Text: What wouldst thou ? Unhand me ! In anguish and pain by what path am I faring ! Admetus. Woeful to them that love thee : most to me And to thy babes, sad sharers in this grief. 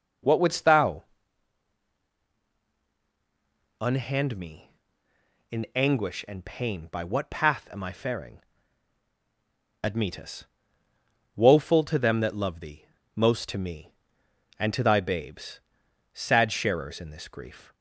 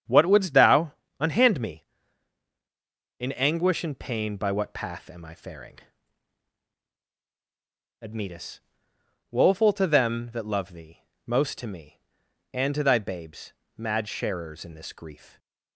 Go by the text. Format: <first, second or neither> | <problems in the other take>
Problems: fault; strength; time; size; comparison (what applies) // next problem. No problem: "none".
first | starts louder than the rest; strong; until 1.3 s; 8 dB // says "mad" for "sad"; at 13.7 s